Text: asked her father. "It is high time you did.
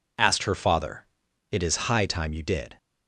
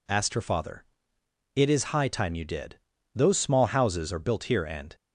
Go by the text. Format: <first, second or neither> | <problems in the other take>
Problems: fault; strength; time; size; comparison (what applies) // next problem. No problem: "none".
first | goes on to say "Those small houses are built here and"; strong; from 3.1 s on; 1.8 s long